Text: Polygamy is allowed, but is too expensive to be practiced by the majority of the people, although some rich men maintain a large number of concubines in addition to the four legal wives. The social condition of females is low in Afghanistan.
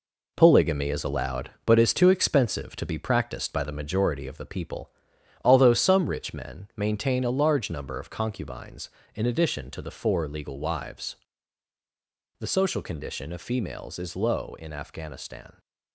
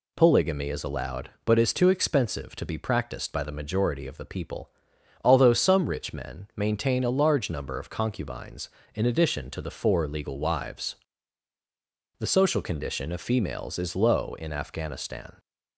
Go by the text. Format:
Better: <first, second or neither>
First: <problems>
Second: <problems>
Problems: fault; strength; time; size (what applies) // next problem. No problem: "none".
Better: second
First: gets quieter; throughout; 7 dB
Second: none